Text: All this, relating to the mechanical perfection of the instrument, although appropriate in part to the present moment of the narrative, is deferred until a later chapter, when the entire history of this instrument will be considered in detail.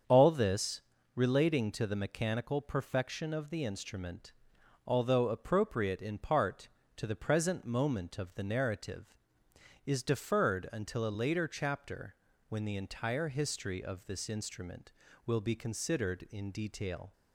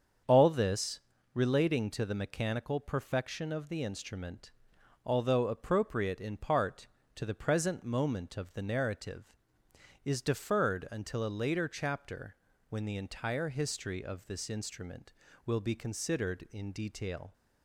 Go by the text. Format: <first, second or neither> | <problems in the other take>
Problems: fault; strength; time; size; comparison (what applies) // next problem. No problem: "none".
neither | starts louder than the rest; strong; the same in both